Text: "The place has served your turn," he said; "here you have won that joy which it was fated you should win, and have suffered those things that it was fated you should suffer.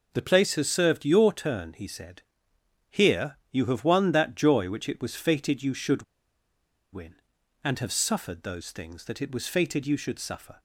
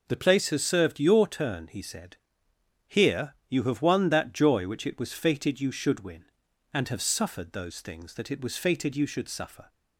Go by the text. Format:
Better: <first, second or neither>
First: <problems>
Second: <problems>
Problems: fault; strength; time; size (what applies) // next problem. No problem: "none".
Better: second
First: pauses between "here" and "you"; slight; at 3.3 s; 0.16 s long // pauses between "should" and "win"; noticeable; at 6.0 s; 0.89 s long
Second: pauses between "here" and "you"; slight; at 3.3 s; 0.16 s long